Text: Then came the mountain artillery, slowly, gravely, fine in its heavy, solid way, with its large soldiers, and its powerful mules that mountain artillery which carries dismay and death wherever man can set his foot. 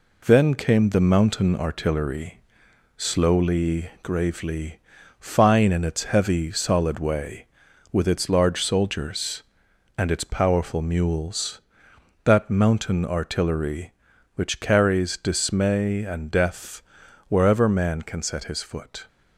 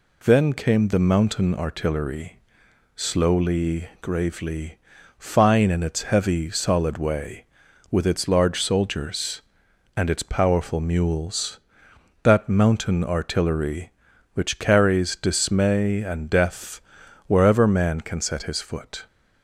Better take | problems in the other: second | gets quieter; noticeable; throughout; 4 dB // pauses between "death" and "wherever"; noticeable; at 16.8 s; 0.46 s long; noticeable in the second

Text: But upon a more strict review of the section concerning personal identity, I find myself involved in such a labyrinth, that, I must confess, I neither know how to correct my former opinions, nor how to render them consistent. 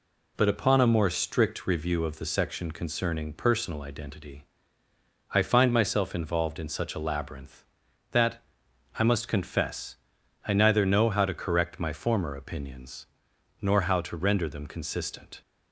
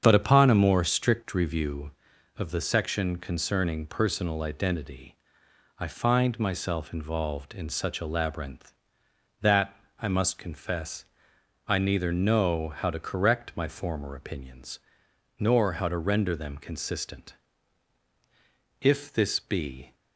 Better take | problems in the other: first | starts louder than the rest; strong; until 1.0 s; 7.5 dB // goes on to say "If this be"; noticeable; from 18.8 s on; 1.1 s long

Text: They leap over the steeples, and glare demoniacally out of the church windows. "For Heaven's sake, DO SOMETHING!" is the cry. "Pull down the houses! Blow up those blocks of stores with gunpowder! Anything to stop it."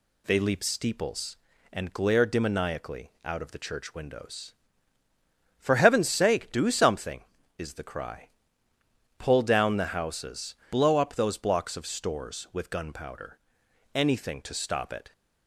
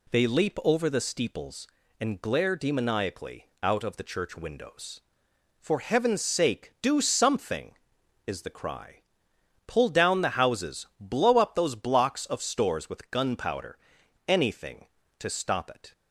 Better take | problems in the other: second | skips "over the"; at 0.6 s

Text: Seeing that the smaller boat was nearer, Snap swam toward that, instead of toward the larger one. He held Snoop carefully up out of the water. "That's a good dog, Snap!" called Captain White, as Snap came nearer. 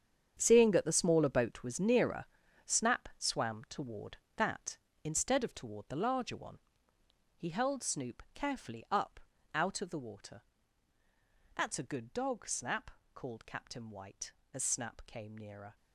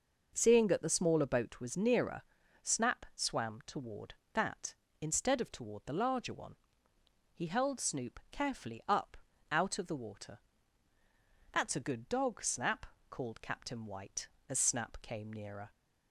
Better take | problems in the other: second | gets quieter; strong; throughout; 13.5 dB // pauses between "up" and "out"; slight; at 9.1 s; 0.36 s long; slight in the second

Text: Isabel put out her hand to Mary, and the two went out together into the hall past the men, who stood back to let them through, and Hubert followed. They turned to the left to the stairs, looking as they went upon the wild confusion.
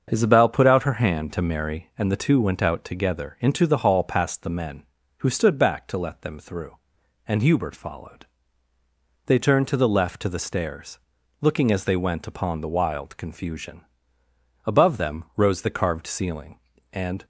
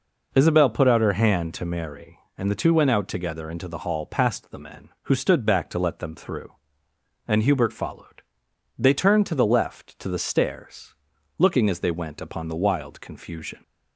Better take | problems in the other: second | starts louder than the rest; until 1.1 s; 6.5 dB // goes on to say "Above them rose the carved ceiling and"; strong; from 14.6 s on; 2.6 s long

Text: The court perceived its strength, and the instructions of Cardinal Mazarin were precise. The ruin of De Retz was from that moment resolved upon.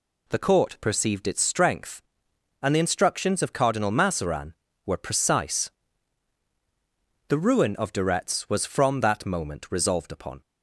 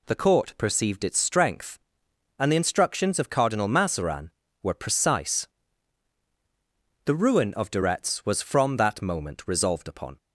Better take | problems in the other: neither | none

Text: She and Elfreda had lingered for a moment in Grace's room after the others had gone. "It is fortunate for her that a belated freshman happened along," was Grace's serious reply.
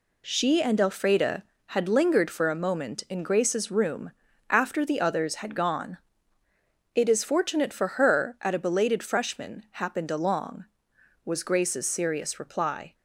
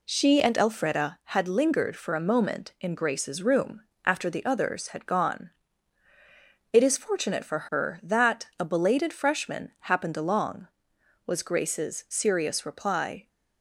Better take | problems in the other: second | pauses between "room" and "after"; at 4.1 s; 0.38 s long; slight in the second // says "at" for "that"; at 8.3 s

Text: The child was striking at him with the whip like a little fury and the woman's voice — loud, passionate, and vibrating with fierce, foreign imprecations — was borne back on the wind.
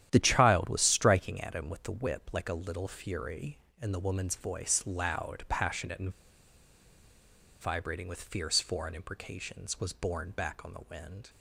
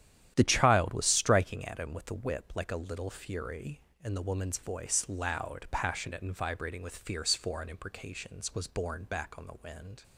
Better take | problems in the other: second | starts louder than the rest; strong; until 1.1 s; 11 dB; strong in the second // pauses between "and" and "vibrating"; strong; at 6.0 s; 1.5 s long

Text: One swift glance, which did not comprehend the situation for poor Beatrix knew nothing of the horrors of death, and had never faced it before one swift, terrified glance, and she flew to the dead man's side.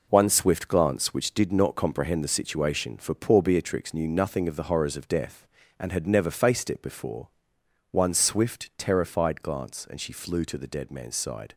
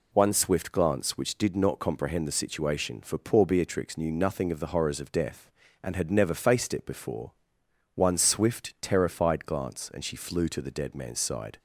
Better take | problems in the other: second | gets quieter; strong; throughout; 7.5 dB // pauses between "before" and "one"; noticeable; at 7.2 s; 0.62 s long; noticeable in the second

